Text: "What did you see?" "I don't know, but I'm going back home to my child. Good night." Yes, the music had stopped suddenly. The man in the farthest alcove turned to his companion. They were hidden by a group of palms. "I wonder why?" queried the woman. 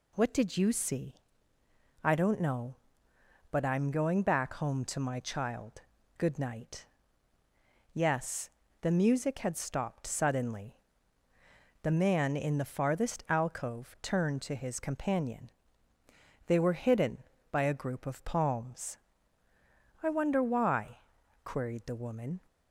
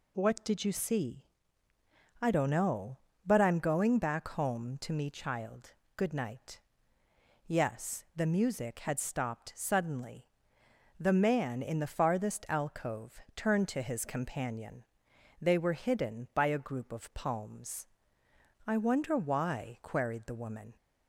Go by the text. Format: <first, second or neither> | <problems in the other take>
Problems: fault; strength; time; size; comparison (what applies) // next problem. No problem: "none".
first | says "me" for "my"; at 4.9 s // pauses between "alcove" and "turned"; slight; at 13.1 s; 0.16 s long